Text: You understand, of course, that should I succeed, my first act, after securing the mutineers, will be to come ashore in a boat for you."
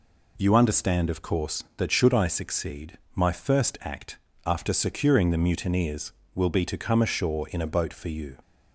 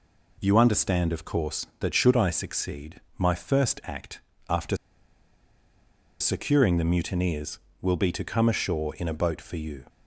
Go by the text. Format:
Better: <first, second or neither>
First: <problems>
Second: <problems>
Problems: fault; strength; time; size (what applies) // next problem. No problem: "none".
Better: first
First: none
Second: pauses between "after" and "securing"; strong; at 4.7 s; 1.4 s long